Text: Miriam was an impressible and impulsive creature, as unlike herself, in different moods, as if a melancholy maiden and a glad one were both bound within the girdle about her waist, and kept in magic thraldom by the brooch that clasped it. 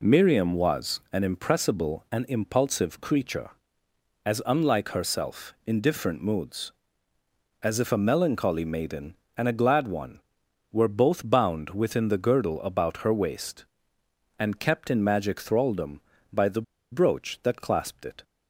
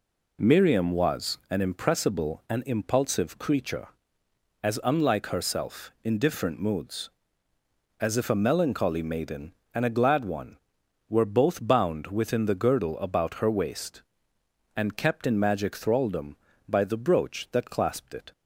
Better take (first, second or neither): second